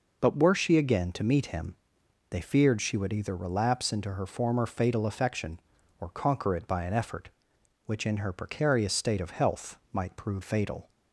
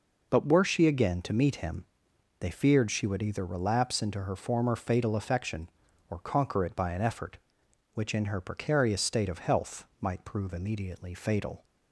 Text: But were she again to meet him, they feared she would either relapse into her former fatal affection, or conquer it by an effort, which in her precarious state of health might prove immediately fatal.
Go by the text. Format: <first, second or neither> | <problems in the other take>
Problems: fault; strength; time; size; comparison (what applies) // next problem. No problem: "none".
second | skips "immediately"; at 10.4 s